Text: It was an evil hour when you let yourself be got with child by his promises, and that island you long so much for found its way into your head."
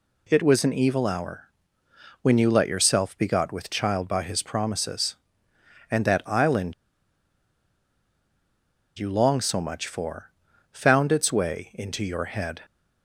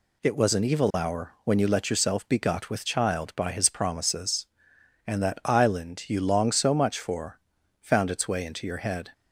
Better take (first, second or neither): second